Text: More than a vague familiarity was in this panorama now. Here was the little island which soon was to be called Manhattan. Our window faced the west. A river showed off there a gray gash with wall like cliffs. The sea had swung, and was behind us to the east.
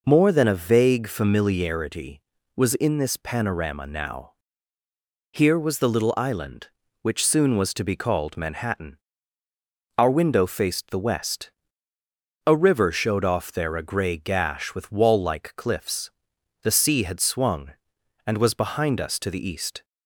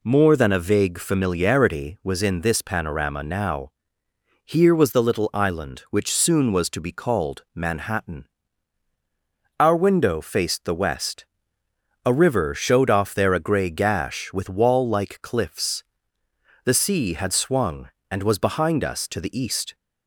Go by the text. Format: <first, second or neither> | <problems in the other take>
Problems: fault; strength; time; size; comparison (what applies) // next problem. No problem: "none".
neither | none